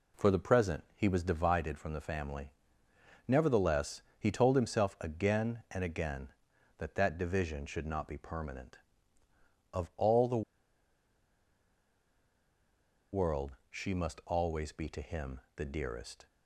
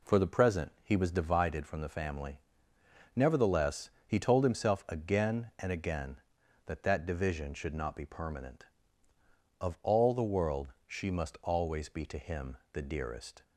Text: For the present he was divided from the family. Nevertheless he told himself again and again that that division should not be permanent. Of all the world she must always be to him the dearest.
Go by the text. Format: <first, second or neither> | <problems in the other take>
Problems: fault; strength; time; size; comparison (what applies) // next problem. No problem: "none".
second | pauses between "Nevertheless" and "he"; slight; at 4.0 s; 0.16 s long; slight in the second // pauses between "the" and "world"; strong; at 10.4 s; 2.7 s long // pauses between "him" and "the"; slight; at 15.4 s; 0.16 s long; slight in the second